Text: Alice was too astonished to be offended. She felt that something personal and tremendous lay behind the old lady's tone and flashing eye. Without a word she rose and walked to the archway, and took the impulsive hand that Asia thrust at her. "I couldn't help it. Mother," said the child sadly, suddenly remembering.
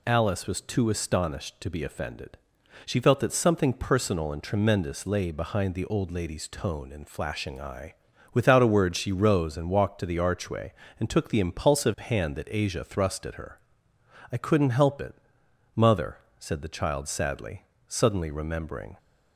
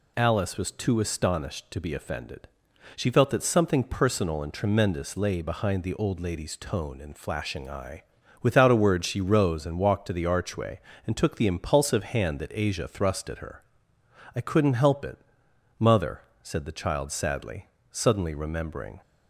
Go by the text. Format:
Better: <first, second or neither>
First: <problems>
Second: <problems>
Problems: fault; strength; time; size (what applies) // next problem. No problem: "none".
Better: neither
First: none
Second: none